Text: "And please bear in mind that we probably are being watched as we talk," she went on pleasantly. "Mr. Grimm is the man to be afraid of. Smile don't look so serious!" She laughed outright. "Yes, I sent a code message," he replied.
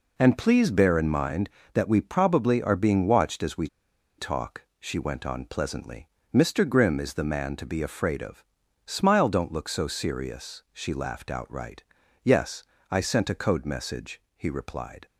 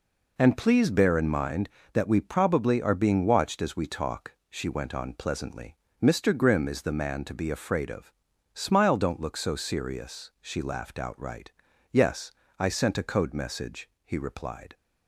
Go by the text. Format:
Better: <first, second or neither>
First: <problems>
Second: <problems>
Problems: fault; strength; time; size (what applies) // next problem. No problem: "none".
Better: second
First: pauses between "we" and "talk"; noticeable; at 3.6 s; 0.51 s long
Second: none